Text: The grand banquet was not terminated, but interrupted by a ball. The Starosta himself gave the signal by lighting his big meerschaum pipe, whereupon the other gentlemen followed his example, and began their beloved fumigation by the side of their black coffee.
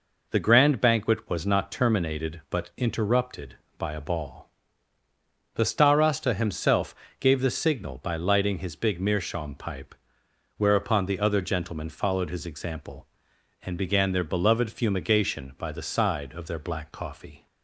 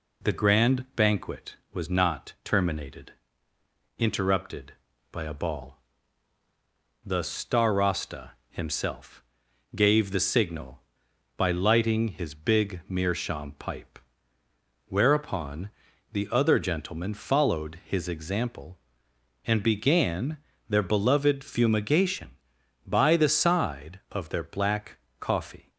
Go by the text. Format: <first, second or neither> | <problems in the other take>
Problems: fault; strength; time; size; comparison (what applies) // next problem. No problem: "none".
first | skips "but"; at 3.5 s // pauses between "Starosta" and "himself"; slight; at 8.2 s; 0.18 s long // pauses between "himself" and "gave"; noticeable; at 9.2 s; 0.50 s long; slight in the first // pauses between "whereupon" and "the"; at 15.6 s; 0.42 s long // pauses between "began" and "their"; slight; at 20.3 s; 0.32 s long // pauses between "black" and "coffee"; slight; at 24.9 s; 0.20 s long